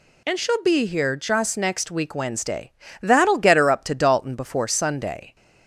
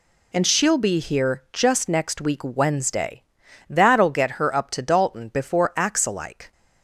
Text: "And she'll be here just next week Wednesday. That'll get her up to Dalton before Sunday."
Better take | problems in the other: first | says "Axelike" for "Sunday"; at 5.7 s

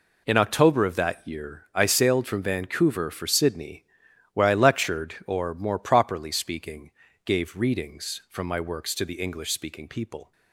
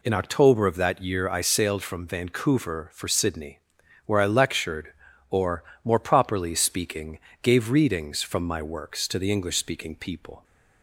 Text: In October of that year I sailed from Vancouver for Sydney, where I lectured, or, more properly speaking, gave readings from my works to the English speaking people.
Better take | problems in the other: neither | none

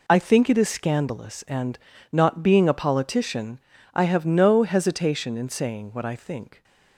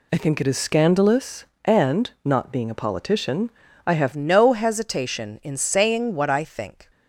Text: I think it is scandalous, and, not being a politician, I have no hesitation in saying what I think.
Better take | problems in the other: first | changes voice at "no"; from 4.1 s on; 2.7 s long

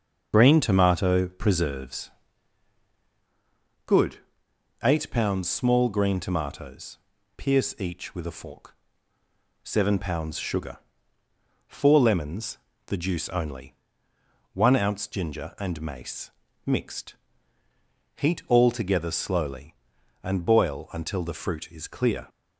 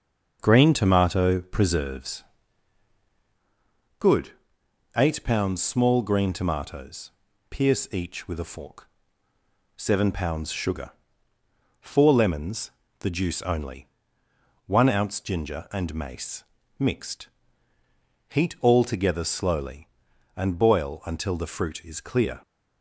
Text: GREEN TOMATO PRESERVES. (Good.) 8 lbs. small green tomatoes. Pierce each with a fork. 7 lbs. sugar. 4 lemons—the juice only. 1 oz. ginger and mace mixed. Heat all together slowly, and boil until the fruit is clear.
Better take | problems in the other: second | loses the start of "GREEN"; at 0.3 s; 55 ms // starts louder than the rest; until 1.3 s; 7 dB; also in the second // pauses between "mace" and "mixed"; slight; at 16.3 s; 0.34 s long; slight in the second

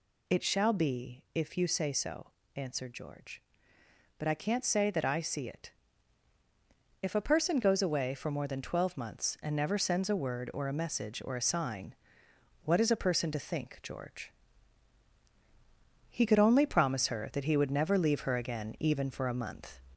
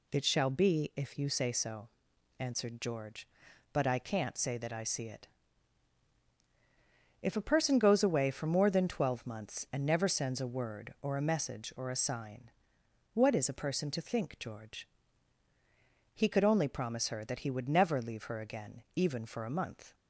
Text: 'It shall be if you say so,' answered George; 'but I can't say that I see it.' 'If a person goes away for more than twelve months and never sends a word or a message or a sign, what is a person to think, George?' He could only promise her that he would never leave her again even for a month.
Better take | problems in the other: second | gets louder; slight; throughout; 3 dB

